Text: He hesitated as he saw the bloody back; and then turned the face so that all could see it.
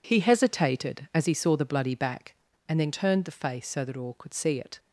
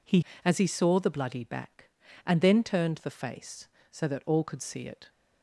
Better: first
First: none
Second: skips "hesitated"; at 0.3 s

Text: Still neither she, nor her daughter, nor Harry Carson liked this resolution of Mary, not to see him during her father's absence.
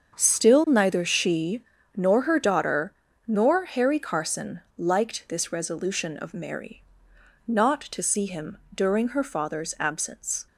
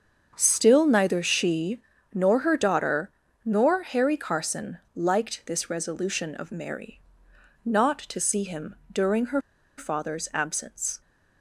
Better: first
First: starts louder than the rest; until 1.2 s; 7 dB // pauses between "Carson" and "liked"; slight; at 4.6 s; 0.18 s long // pauses between "him" and "during"; slight; at 8.5 s; 0.18 s long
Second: starts louder than the rest; until 1.3 s; 7 dB // pauses between "Carson" and "liked"; slight; at 4.7 s; 0.18 s long // pauses between "him" and "during"; slight; at 8.7 s; 0.18 s long // pauses between "her" and "father's"; at 9.4 s; 0.37 s long

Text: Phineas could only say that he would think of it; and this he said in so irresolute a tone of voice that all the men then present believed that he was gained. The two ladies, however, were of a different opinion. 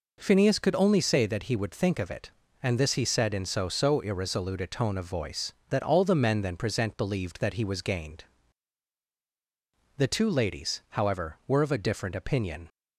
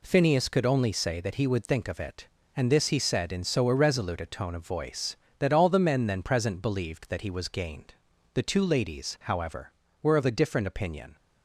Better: second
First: says "so" twice; at 3.6 s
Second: none

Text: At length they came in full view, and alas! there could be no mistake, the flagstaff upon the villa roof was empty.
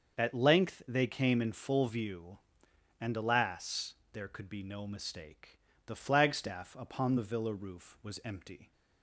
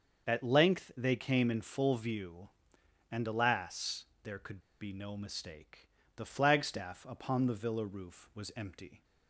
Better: first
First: starts louder than the rest; until 1.2 s; 6.5 dB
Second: starts louder than the rest; until 1.3 s; 6.5 dB // pauses between "could" and "be"; slight; at 4.6 s; 0.20 s long

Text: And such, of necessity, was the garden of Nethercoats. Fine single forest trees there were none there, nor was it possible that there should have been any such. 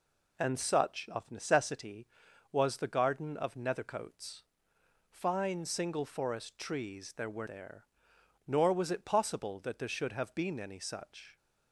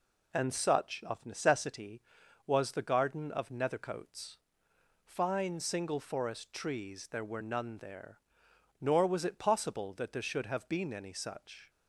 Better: second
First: skips "none"; at 7.4 s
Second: none

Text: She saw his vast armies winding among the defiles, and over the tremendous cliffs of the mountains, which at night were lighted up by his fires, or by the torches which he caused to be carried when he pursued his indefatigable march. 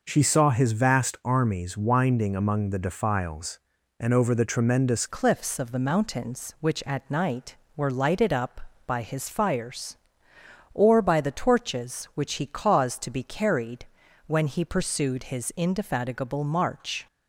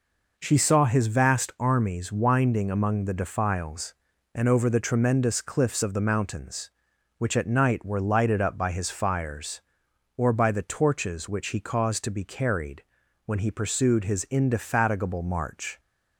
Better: second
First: changes voice at "cliffs"; from 5.0 s on; 12.0 s long // pauses between "carried" and "when"; at 13.8 s; 0.40 s long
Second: pauses between "carried" and "when"; at 12.8 s; 0.42 s long

